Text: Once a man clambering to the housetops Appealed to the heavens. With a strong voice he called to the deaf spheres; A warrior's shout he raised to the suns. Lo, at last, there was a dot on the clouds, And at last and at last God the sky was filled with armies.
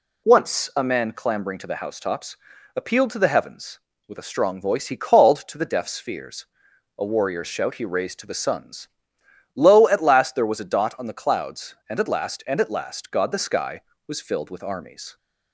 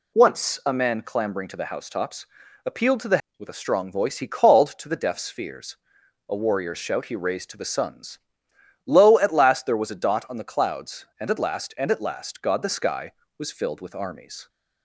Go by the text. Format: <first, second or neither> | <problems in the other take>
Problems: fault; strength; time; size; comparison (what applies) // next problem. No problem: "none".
first | pauses between "housetops" and "Appealed"; at 2.2 s; 0.40 s long; also in the first // skips "heavens"; at 3.2 s